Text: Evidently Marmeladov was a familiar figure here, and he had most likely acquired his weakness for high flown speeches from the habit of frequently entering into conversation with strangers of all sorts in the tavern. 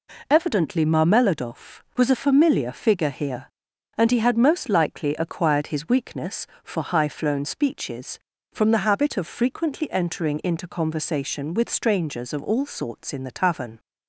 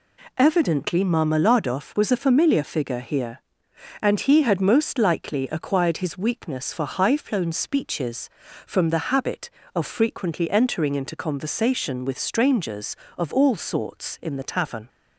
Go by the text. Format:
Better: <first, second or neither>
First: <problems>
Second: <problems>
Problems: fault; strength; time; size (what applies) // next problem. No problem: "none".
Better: neither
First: none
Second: none